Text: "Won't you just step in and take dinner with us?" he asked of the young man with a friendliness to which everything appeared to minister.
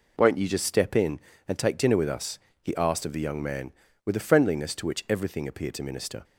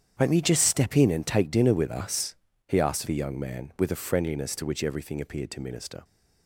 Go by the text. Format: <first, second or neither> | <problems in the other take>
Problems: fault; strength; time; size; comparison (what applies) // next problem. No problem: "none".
first | starts louder than the rest; strong; until 1.1 s; 8.5 dB // skips "of"; at 3.0 s